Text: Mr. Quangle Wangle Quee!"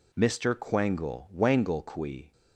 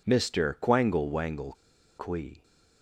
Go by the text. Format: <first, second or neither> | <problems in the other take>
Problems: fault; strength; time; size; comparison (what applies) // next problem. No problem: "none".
first | pauses between "Wangle" and "Quee"; at 1.5 s; 0.44 s long